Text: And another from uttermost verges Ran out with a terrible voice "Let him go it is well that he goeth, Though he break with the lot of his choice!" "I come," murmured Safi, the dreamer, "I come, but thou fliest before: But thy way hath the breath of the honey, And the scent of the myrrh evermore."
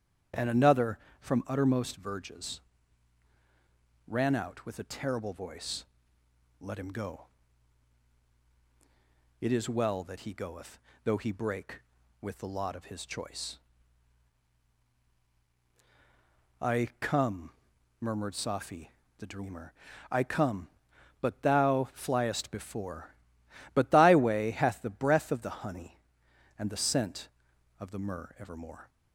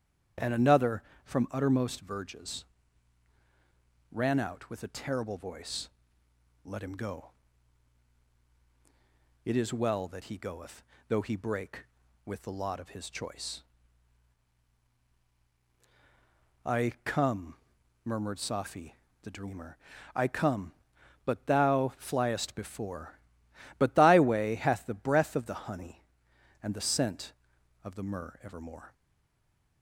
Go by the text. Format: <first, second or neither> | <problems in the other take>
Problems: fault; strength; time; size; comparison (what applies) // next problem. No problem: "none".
first | starts louder than the rest; strong; until 1.6 s; 8.5 dB; strong in the first // pauses between "verges" and "Ran"; strong; at 2.6 s; 1.4 s long; strong in the first // pauses between "voice" and "Let"; noticeable; at 5.8 s; 0.76 s long; noticeable in the first // pauses between "go" and "it"; strong; at 7.3 s; 2.1 s long; strong in the first // stays silent after the last word; slight; from 28.9 s on; 0.9 s long